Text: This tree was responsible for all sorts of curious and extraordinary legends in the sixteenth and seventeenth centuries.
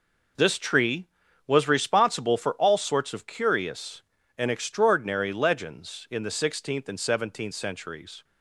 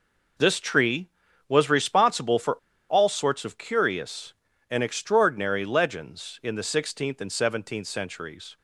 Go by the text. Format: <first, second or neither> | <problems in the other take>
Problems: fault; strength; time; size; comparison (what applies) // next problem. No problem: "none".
first | pauses between "for" and "all"; slight; at 2.5 s; 0.32 s long